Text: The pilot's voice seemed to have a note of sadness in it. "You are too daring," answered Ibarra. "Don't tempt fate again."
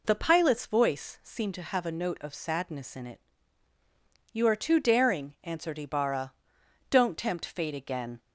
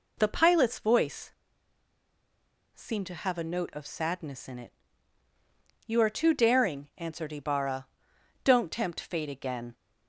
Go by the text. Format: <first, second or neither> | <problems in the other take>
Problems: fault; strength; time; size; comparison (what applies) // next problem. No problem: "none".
first | pauses between "voice" and "seemed"; strong; at 1.3 s; 1.4 s long